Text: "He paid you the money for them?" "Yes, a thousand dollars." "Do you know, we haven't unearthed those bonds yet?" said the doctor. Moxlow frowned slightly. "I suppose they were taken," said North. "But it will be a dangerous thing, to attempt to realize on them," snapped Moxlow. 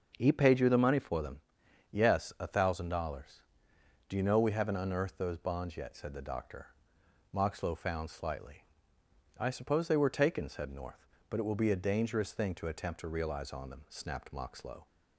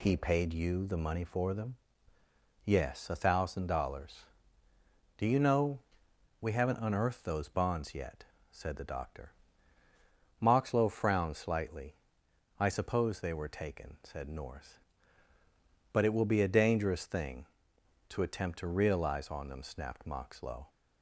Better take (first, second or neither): second